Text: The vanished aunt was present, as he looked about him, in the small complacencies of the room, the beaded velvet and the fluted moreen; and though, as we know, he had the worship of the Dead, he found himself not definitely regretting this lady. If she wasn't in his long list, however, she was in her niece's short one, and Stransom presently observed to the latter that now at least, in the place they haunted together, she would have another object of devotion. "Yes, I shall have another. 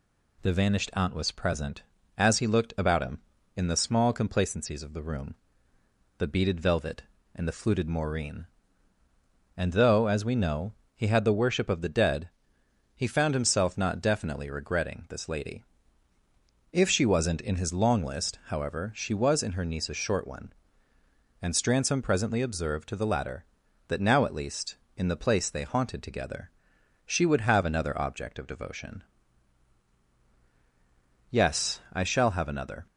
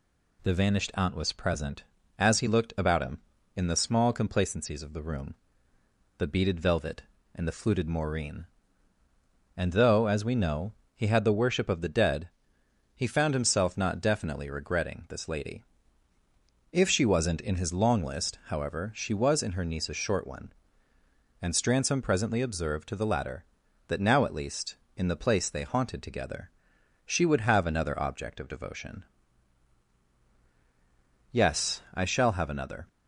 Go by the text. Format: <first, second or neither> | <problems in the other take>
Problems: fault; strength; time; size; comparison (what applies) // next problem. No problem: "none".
neither | none